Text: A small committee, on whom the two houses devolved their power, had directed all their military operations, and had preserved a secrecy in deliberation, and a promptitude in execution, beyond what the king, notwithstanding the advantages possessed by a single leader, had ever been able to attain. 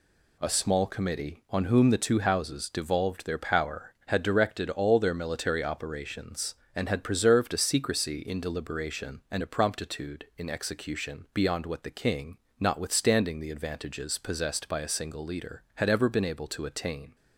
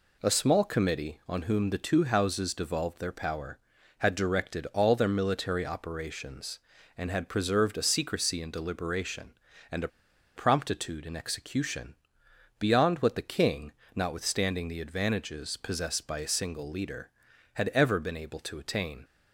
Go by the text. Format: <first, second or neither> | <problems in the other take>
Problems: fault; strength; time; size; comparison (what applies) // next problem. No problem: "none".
first | pauses between "a" and "promptitude"; noticeable; at 9.8 s; 0.47 s long